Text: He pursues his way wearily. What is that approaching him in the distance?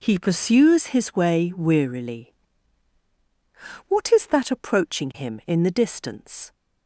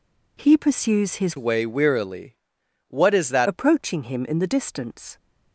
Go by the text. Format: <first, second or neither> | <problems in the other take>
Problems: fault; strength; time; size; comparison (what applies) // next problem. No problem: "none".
first | changes voice from "way" to "that"; from 1.3 to 3.4 s; 2.1 s long